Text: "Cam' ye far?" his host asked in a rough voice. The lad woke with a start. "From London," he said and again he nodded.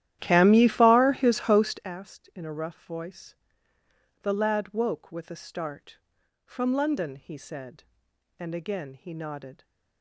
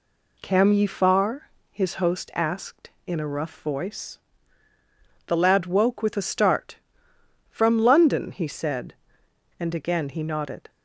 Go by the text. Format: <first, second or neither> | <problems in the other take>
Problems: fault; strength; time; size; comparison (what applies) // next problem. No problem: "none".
second | starts louder than the rest; strong; until 1.9 s; 12.5 dB